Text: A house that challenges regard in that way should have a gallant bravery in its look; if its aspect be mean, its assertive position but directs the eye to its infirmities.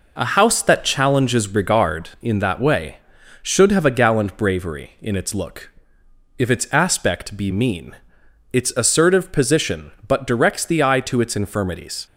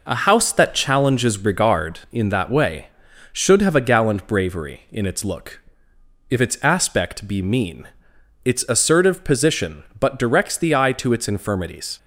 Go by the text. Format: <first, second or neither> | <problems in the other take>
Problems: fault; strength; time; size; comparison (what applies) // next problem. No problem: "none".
neither | none